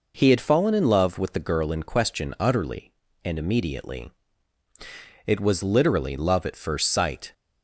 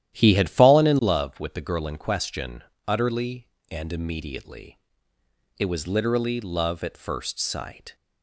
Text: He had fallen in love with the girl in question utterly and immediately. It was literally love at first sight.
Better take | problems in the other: first | starts louder than the rest; strong; until 1.2 s; 12 dB // pauses between "question" and "utterly"; slight; at 2.6 s; 0.24 s long

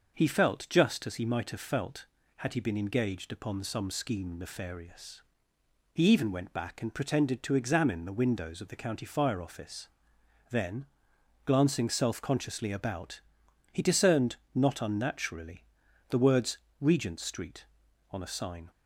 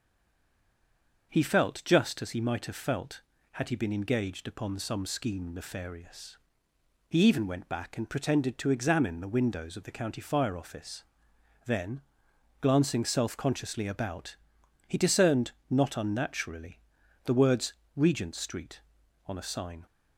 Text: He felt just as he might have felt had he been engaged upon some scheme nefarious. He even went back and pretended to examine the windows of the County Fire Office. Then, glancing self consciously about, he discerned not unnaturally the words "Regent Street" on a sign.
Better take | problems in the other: first | stays silent before the first word; noticeable; until 1.3 s; 1.3 s long // starts louder than the rest; until 2.3 s; 6 dB; also in the first // pauses between "discerned" and "not"; slight; at 15.5 s; 0.18 s long; slight in the first // pauses between "unnaturally" and "the"; noticeable; at 16.7 s; 0.46 s long; noticeable in the first // pauses between "words" and "Regent"; slight; at 17.7 s; 0.22 s long; slight in the first

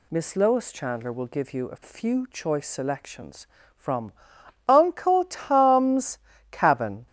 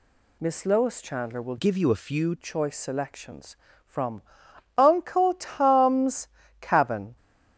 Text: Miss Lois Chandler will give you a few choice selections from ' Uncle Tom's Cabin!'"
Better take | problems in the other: first | changes voice from "give" to "few"; from 1.5 to 2.3 s; 0.8 s long // pauses between "Tom's" and "Cabin"; slight; at 6.2 s; 0.32 s long; slight in the first

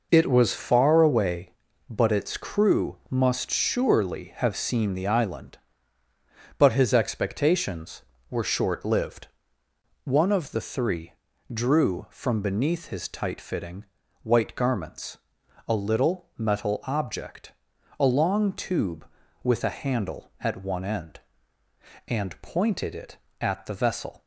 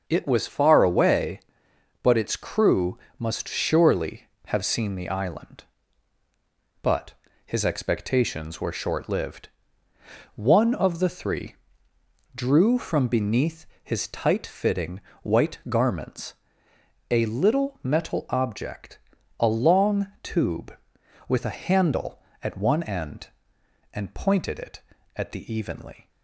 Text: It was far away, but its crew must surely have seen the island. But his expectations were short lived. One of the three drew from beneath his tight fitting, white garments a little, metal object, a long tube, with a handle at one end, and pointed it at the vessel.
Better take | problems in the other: first | starts louder than the rest; until 1.0 s; 6.5 dB // pauses between "crew" and "must"; slight; at 2.9 s; 0.20 s long // pauses between "But" and "his"; slight; at 7.1 s; 0.32 s long // pauses between "three" and "drew"; noticeable; at 11.5 s; 0.80 s long; also in the first // pauses between "beneath" and "his"; slight; at 13.6 s; 0.16 s long // pauses between "garments" and "a"; noticeable; at 16.3 s; 0.76 s long; noticeable in the first // pauses between "long" and "tube"; slight; at 20.0 s; 0.16 s long // says "evenly" for "vessel"; at 25.5 s

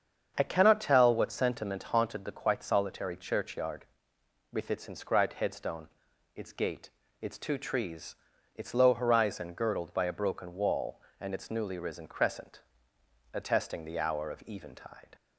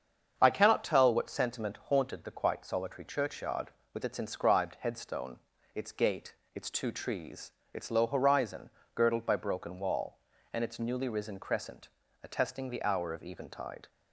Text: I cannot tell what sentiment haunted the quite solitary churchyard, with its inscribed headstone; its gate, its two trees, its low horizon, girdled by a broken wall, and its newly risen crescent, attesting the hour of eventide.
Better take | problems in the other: first | starts louder than the rest; strong; until 1.3 s; 7 dB; strong in the first // skips "a"; at 9.3 s

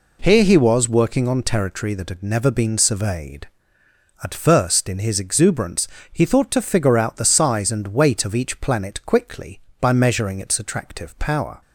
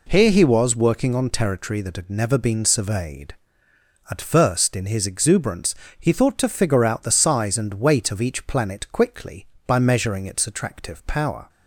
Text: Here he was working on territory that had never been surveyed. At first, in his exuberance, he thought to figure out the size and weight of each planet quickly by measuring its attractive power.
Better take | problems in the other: neither | none

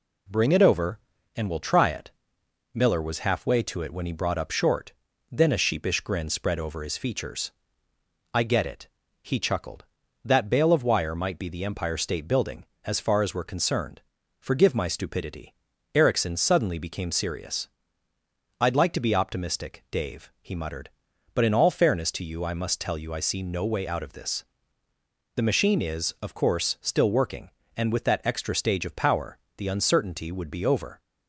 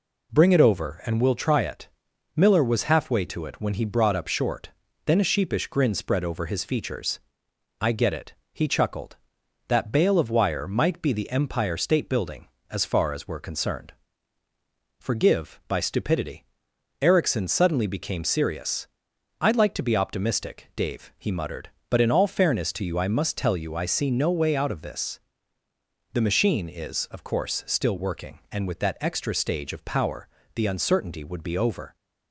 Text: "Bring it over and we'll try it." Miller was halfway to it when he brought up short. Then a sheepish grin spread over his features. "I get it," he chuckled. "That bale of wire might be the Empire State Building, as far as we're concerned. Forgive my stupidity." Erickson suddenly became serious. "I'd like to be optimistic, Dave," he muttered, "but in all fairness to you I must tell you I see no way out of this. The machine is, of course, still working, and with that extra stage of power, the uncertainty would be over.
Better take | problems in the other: first | says "by" for "my"; at 15.6 s

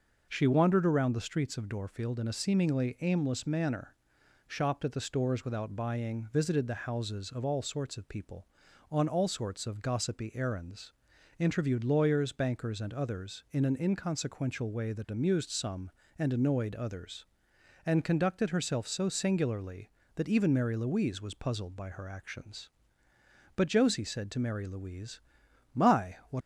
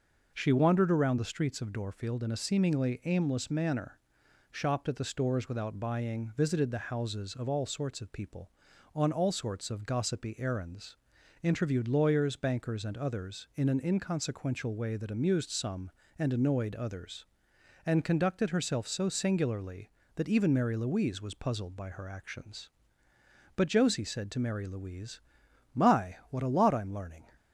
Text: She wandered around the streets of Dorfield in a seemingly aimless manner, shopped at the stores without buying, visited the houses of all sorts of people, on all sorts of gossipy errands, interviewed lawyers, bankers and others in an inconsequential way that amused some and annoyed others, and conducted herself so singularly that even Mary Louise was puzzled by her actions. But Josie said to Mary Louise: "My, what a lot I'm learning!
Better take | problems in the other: second | stops before "a lot I'm learning"; at 26.4 s

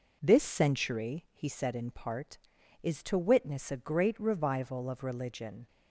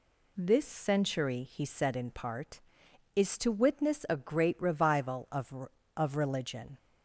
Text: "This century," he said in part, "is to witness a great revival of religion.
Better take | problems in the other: first | says "of" twice; at 5.9 s

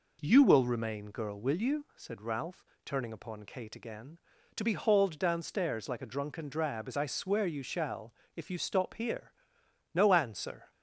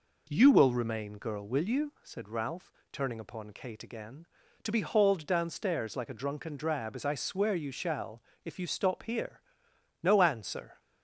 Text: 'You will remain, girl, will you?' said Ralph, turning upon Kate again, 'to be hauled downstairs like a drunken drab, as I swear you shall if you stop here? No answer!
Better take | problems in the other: neither | pauses between "shall" and "if"; slight; the same in both

